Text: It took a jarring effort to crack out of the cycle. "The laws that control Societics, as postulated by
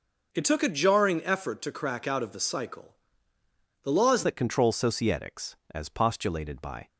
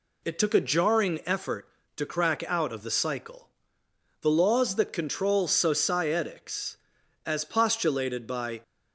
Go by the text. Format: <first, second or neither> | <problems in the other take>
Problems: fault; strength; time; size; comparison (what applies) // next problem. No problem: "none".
second | changes voice at "that"; from 4.2 s on; 2.6 s long